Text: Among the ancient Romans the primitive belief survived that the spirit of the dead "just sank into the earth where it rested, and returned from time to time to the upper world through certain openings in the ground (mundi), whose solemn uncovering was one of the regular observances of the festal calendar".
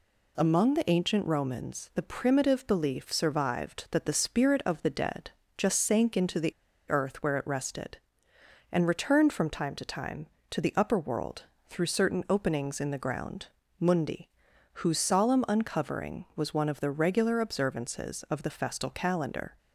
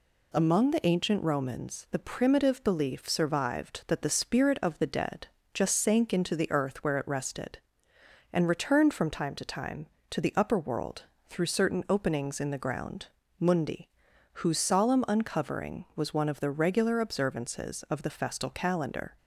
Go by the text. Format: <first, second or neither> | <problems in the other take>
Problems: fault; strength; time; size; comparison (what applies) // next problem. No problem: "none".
second | pauses between "dead" and "just"; slight; at 5.3 s; 0.26 s long; slight in the second // pauses between "the" and "earth"; at 6.5 s; 0.36 s long // pauses between "world" and "through"; slight; at 11.4 s; 0.24 s long; slight in the second